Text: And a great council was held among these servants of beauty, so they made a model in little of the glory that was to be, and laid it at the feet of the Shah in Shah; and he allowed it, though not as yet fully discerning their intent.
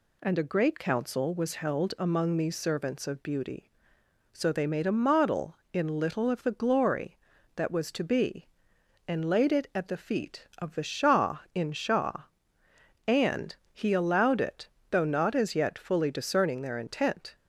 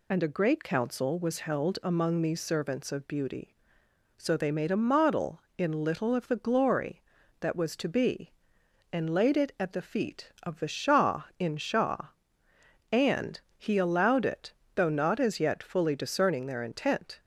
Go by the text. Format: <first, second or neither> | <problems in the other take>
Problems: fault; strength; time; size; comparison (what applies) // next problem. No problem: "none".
first | loses the start of "And"; at 0.1 s; 45 ms // pauses between "and" and "he"; slight; at 13.3 s; 0.18 s long; slight in the first